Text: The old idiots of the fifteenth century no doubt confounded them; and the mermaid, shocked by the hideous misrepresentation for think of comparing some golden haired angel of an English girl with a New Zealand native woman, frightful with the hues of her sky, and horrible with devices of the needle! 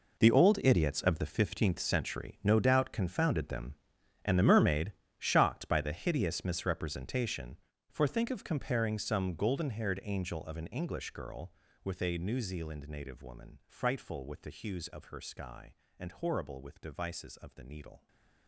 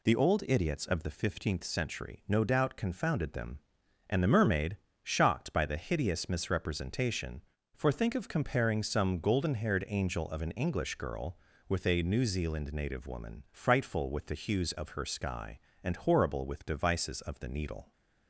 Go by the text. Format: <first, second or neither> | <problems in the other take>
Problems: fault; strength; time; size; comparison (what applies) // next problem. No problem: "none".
second | gets quieter; strong; throughout; 15.5 dB // stays silent after the last word; slight; from 17.9 s on; 0.5 s long